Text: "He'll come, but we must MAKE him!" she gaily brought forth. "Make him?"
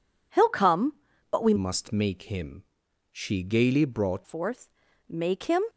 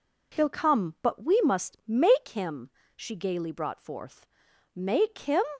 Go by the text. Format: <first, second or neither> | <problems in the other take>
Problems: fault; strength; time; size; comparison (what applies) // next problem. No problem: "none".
second | changes voice from "must" to "brought"; from 1.5 to 4.2 s; 2.7 s long